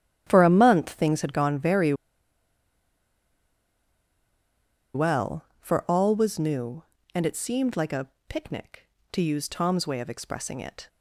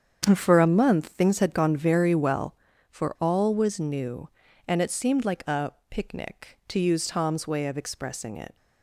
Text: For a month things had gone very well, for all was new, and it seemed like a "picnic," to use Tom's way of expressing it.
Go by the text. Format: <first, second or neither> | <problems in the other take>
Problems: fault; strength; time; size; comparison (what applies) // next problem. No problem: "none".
second | starts louder than the rest; strong; until 1.2 s; 11.5 dB; strong in the second // pauses between "very" and "well"; strong; at 1.9 s; 3.0 s long // pauses between "a" and "picnic"; slight; at 8.0 s; 0.22 s long; slight in the second